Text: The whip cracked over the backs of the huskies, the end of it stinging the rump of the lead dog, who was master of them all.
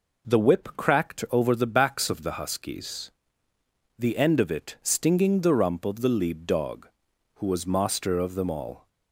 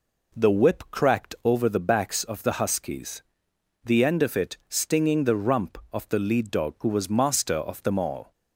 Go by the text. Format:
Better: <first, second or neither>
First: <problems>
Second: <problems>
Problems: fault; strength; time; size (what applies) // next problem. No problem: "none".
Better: neither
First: none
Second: none